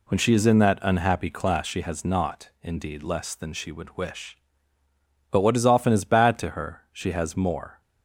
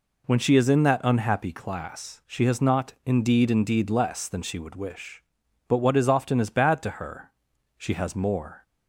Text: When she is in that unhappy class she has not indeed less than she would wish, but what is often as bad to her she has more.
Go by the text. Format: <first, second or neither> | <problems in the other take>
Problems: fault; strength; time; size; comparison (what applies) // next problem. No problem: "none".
first | says "indeed" twice; at 3.5 s // pauses between "her" and "she"; noticeable; at 7.3 s; 0.46 s long